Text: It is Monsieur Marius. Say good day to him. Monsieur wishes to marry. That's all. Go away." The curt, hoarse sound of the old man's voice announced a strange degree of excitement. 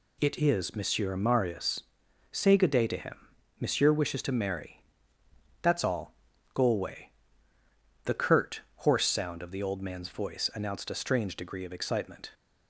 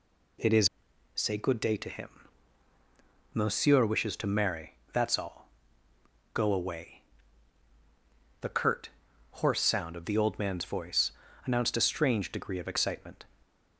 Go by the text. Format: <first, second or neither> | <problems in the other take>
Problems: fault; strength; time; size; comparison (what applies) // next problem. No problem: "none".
first | skips "Monsieur Marius"; at 0.9 s // pauses between "voice" and "announced"; slight; at 11.1 s; 0.34 s long